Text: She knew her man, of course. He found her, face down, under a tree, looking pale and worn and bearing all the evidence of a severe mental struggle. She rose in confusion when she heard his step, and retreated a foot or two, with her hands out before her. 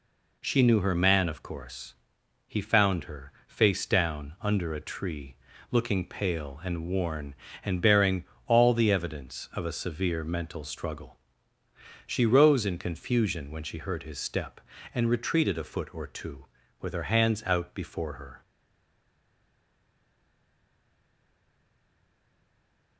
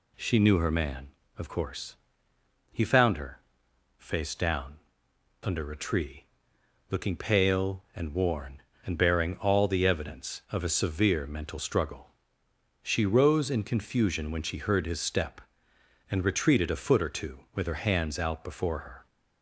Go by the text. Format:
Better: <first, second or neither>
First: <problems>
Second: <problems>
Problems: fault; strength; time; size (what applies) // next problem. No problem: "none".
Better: second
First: pauses between "bearing" and "all"; slight; at 8.2 s; 0.22 s long // stays silent after the last word; strong; from 18.4 s on; 4.5 s long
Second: none